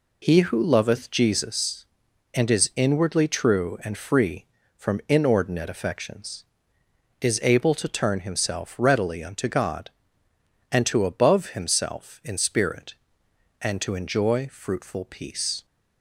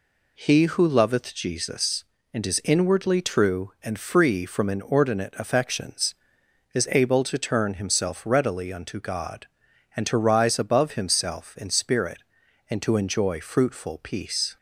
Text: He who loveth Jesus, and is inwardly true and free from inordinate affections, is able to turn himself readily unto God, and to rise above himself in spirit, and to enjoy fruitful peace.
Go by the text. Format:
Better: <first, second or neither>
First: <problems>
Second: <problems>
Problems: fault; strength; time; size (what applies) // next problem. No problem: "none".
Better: second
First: skips "rise"; at 11.0 s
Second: none